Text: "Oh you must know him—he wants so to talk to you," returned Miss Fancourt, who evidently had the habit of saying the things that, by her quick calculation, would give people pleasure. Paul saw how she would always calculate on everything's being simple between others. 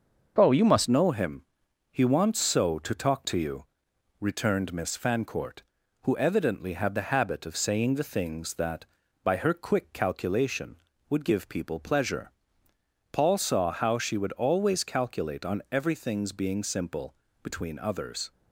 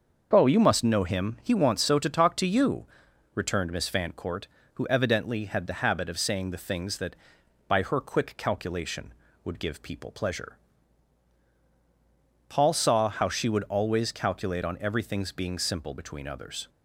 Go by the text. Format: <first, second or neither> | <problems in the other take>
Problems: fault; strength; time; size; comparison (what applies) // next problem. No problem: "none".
second | starts louder than the rest; until 1.3 s; 6 dB; also in the second // changes voice at "know"; from 0.8 s on; 17.5 s long // pauses between "simple" and "between"; slight; at 17.1 s; 0.30 s long